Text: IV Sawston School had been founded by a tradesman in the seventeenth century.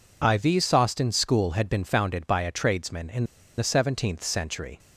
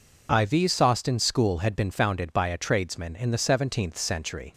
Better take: second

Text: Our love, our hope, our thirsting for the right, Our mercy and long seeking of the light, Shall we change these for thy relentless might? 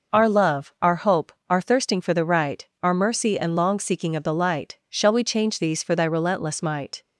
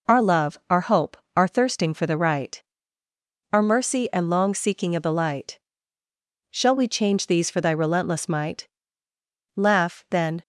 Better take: first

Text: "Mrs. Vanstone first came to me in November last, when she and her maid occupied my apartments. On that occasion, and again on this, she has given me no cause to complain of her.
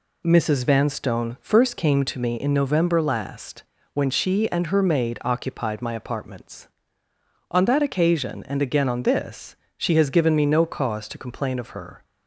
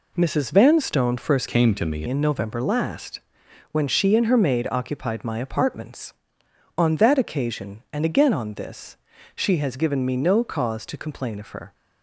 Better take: first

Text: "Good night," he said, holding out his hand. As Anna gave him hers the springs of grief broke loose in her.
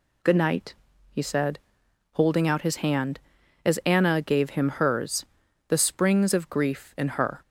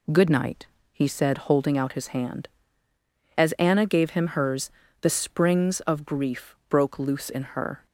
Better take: second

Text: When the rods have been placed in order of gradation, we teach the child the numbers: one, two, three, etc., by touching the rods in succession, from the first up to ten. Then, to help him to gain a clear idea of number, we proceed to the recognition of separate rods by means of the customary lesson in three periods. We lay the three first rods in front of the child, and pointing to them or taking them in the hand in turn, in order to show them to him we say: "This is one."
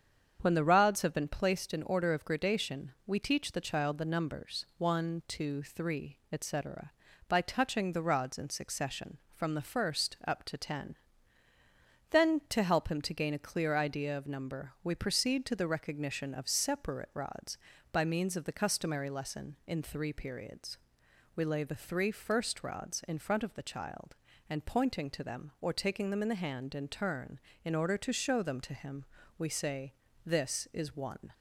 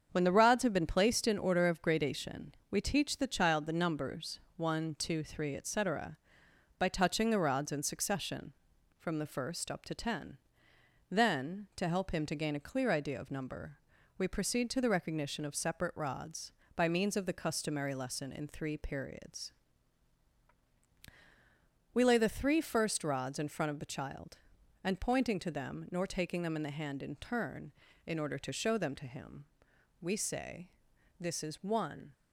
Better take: first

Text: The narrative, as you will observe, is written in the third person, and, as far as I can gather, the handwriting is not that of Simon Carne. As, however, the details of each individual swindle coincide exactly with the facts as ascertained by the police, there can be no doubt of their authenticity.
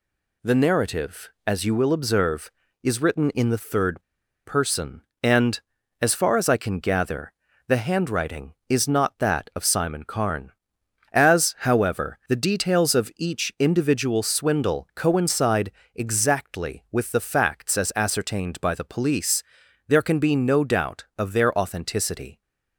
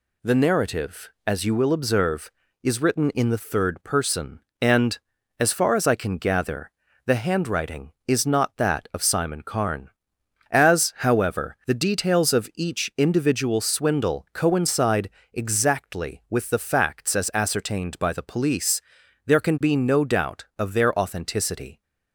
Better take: second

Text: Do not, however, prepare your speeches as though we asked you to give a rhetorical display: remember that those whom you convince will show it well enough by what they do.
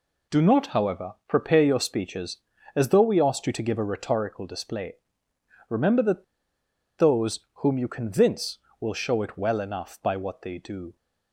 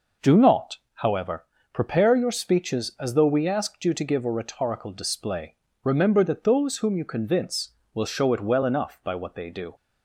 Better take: second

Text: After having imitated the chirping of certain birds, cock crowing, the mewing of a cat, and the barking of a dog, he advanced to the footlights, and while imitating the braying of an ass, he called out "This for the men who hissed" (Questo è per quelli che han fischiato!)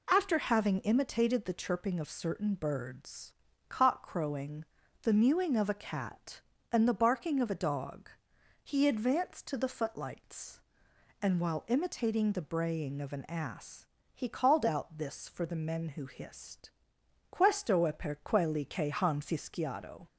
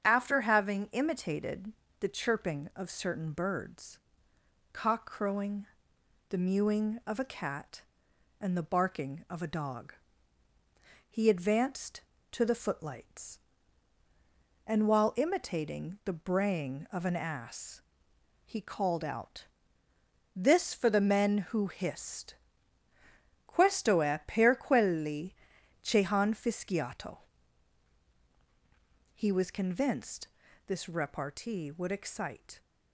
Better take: first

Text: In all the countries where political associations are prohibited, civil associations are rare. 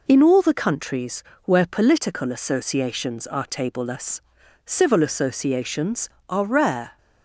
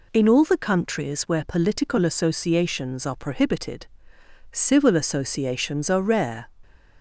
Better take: second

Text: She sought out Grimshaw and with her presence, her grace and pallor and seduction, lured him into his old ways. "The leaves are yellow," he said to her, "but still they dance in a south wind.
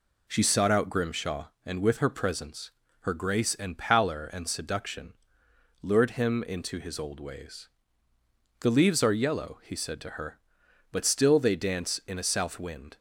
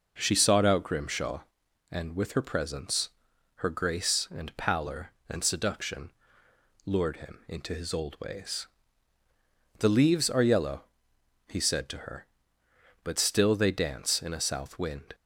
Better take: neither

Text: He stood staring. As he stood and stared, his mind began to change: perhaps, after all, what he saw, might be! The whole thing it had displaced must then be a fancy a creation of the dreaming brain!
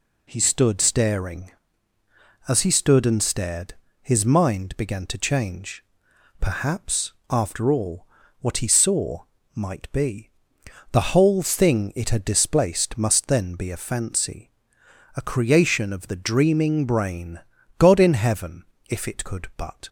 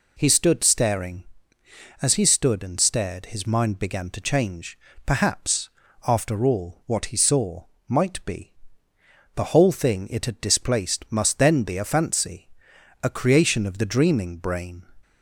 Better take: second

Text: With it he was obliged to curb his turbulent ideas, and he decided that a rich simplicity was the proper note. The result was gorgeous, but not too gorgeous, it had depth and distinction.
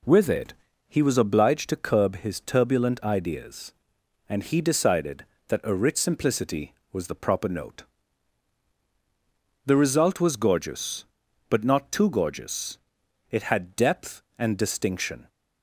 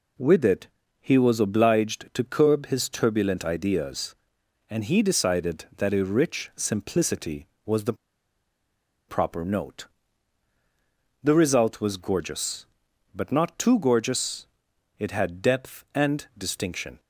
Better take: first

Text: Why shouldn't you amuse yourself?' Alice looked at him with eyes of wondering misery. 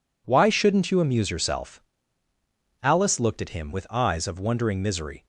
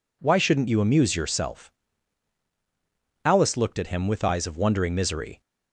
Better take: neither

